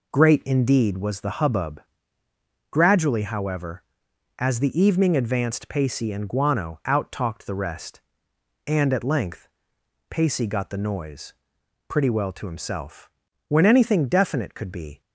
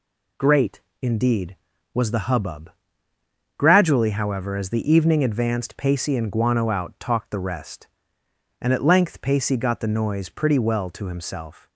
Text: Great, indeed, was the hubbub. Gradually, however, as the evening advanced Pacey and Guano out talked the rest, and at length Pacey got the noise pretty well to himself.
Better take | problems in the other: second | pauses between "length" and "Pacey"; noticeable; at 9.4 s; 0.60 s long // pauses between "noise" and "pretty"; noticeable; at 11.3 s; 0.56 s long // goes on to say "When anything definite could be"; from 13.4 s on; 1.5 s long

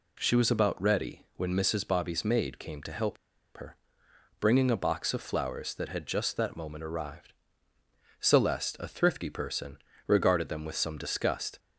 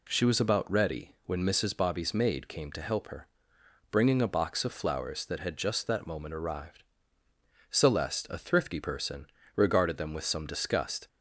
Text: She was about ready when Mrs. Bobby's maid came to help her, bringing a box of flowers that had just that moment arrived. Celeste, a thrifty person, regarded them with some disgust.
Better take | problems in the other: second | pauses between "help" and "her"; at 3.1 s; 0.39 s long

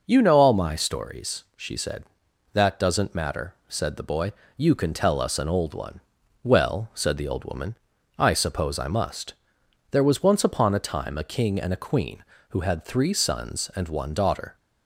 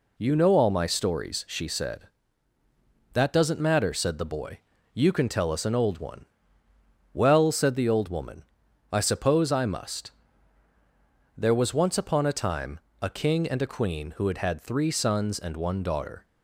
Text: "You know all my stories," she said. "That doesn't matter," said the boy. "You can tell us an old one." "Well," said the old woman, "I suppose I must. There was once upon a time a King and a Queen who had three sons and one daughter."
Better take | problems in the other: first | pauses between "time" and "a"; slight; at 12.7 s; 0.24 s long // says "had" twice; at 14.3 s

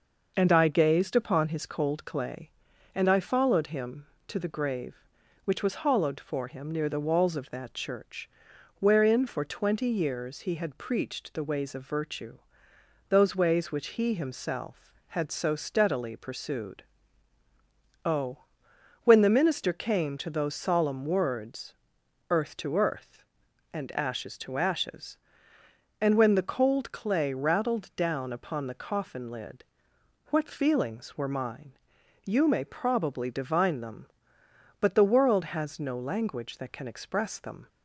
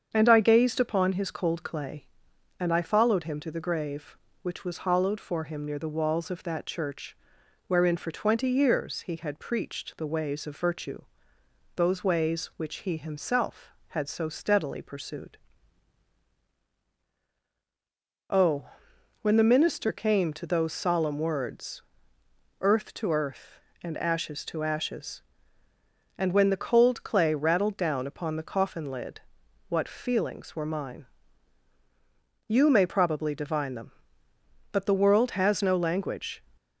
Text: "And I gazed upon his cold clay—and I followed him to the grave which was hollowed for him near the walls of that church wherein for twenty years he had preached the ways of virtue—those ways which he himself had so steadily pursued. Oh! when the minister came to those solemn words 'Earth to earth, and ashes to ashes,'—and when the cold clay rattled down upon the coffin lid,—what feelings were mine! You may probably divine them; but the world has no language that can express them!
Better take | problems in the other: first | starts louder than the rest; strong; until 1.1 s; 7.5 dB // pauses between "church" and "wherein"; noticeable; at 7.1 s; 0.52 s long; noticeable in the first // pauses between "words" and "Earth"; noticeable; at 21.8 s; 0.78 s long; noticeable in the first // stops before "that can express them"; at 36.5 s

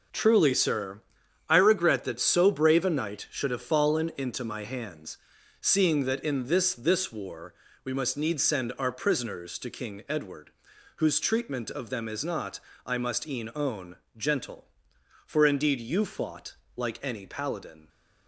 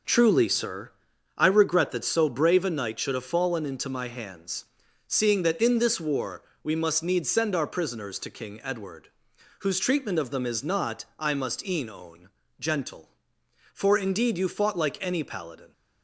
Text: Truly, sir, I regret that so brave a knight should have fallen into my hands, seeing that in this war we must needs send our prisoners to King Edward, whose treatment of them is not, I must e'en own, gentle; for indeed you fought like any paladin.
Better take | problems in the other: second | says "this" twice; at 6.7 s // pauses between "war" and "we"; slight; at 7.5 s; 0.30 s long; slight in the second // pauses between "fought" and "like"; slight; at 16.5 s; 0.20 s long

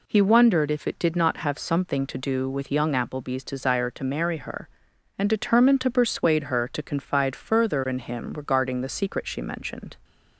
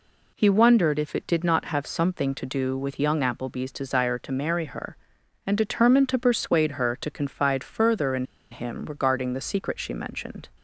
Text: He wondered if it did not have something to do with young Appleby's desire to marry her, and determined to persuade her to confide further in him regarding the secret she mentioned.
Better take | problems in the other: first | pauses between "in" and "him"; slight; at 8.2 s; 0.26 s long

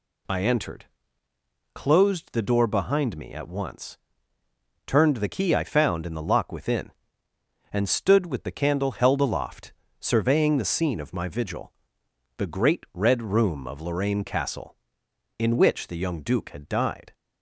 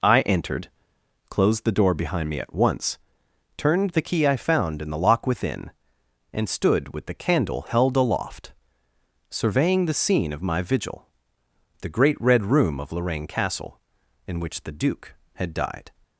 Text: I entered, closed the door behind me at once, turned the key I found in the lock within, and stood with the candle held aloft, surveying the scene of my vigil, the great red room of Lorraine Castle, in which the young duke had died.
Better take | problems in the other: first | skips "young"; at 14.7 s

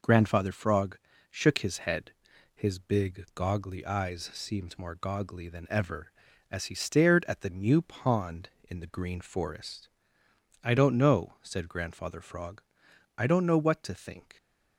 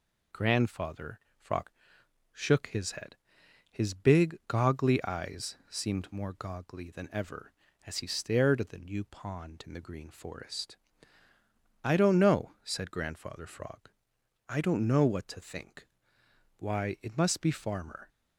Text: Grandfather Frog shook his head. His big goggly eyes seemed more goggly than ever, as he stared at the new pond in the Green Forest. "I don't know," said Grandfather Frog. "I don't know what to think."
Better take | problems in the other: first | pauses between "Grandfather" and "Frog"; slight; at 1.1 s; 0.20 s long // pauses between "Frog" and "shook"; noticeable; at 1.6 s; 0.64 s long; slight in the first // goes on to say "Why it must be Farmer"; from 16.5 s on; 1.5 s long

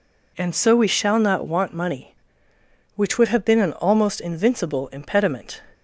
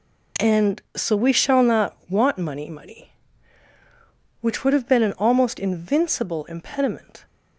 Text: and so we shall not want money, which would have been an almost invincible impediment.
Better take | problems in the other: first | says "money" twice; at 2.6 s

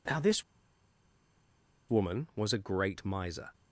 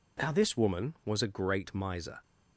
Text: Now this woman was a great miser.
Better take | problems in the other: second | pauses between "this" and "woman"; strong; at 0.4 s; 1.4 s long

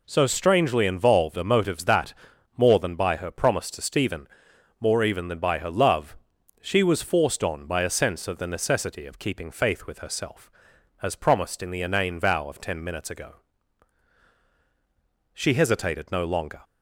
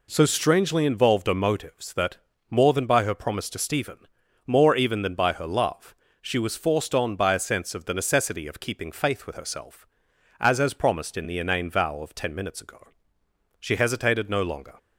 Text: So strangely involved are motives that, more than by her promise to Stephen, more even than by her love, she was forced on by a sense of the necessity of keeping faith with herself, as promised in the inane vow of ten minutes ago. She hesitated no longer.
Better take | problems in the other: first | says "as" twice; at 10.6 s

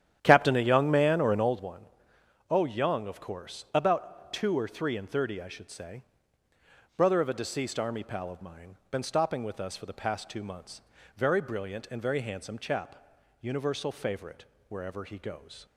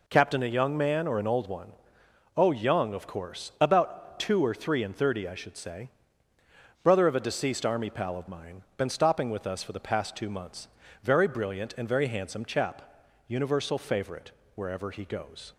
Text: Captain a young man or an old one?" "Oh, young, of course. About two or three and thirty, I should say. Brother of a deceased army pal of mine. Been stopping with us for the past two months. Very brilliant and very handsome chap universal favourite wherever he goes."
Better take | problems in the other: second | starts louder than the rest; strong; until 1.6 s; 10.5 dB // pauses between "chap" and "universal"; at 12.9 s; 0.44 s long; also in the second // pauses between "favourite" and "wherever"; slight; at 14.4 s; 0.24 s long; slight in the second

